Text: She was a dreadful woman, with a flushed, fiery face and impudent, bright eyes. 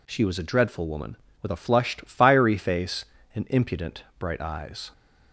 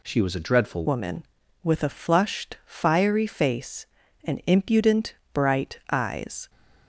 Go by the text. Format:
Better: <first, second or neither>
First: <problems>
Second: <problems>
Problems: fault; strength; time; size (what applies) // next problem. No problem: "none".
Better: first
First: none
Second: changes voice at "woman"; from 0.8 s on; 5.6 s long